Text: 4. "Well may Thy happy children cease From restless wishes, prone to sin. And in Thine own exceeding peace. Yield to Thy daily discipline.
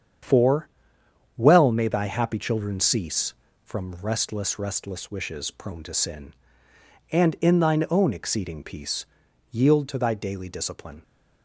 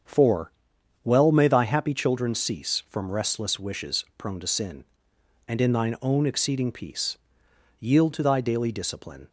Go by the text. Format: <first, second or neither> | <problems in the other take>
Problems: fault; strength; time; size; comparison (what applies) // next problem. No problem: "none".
second | starts louder than the rest; strong; until 1.9 s; 8 dB; strong in the second // says "restless" twice; at 4.5 s